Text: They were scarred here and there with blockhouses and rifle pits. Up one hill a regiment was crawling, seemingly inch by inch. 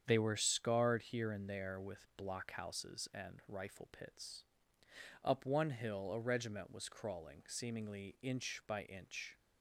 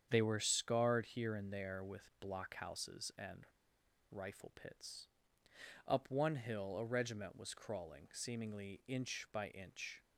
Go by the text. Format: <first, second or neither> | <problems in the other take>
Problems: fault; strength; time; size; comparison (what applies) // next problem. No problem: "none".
first | starts louder than the rest; strong; until 1.1 s; 8 dB; strong in the first // pauses between "and" and "rifle"; noticeable; at 3.4 s; 0.67 s long